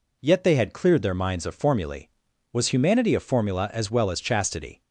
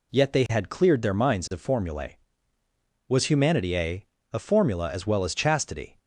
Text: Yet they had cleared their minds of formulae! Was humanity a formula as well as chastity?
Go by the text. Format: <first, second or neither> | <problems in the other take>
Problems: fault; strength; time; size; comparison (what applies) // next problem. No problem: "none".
first | says "a" twice; at 4.3 s